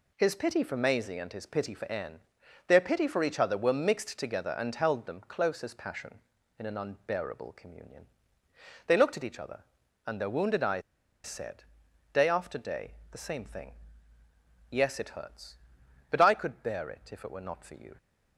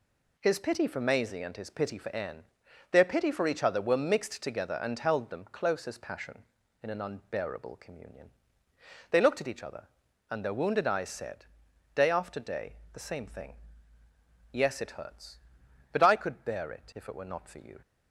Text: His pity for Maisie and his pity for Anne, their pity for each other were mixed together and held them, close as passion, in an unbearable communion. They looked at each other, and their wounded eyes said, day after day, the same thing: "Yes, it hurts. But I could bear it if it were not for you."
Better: second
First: pauses between "eyes" and "said"; at 10.8 s; 0.45 s long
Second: none

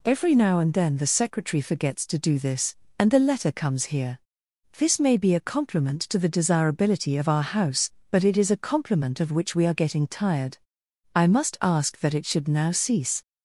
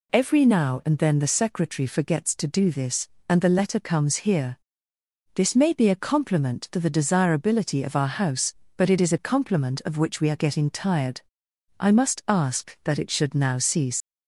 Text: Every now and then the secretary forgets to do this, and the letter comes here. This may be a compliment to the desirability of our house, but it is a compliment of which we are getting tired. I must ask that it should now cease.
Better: first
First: none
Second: leaves "cease" unfinished; at 14.0 s; 95 ms

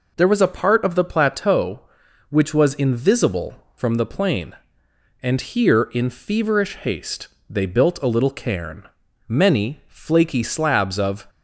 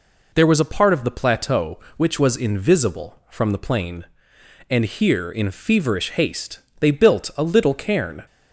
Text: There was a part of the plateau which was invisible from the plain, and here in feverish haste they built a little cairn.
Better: second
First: pauses between "haste" and "they"; slight; at 7.2 s; 0.20 s long // goes on to say "Many flaky slabs of"; strong; from 9.2 s on; 1.9 s long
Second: pauses between "haste" and "they"; slight; at 6.5 s; 0.20 s long

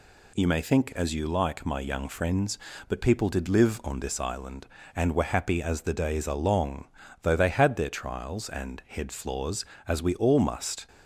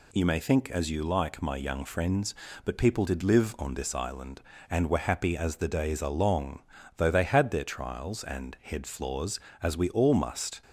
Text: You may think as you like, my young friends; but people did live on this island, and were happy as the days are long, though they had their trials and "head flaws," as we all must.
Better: neither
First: none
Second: none

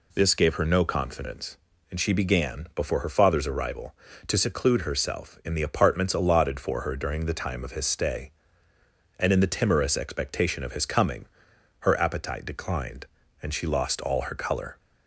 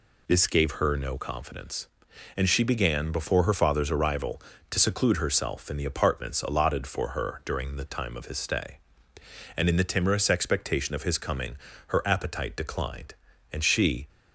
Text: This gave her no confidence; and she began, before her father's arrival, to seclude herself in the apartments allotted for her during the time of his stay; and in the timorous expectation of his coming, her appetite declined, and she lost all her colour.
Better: first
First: none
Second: stops before "lost all her colour"; at 14.0 s

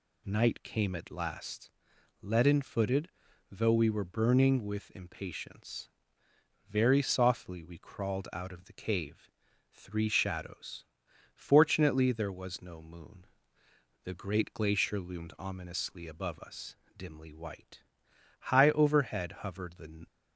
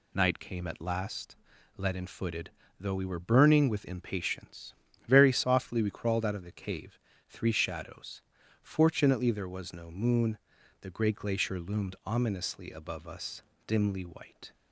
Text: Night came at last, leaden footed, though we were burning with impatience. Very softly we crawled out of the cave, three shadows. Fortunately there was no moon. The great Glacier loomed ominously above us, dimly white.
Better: second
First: goes on to say "High overhead hovered the"; from 18.4 s on; 1.6 s long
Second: none

